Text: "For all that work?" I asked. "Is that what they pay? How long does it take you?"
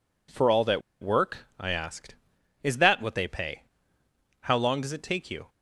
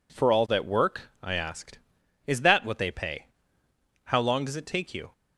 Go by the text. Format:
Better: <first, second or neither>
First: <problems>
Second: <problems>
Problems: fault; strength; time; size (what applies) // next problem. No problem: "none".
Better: second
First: pauses between "that" and "work"; slight; at 0.8 s; 0.21 s long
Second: none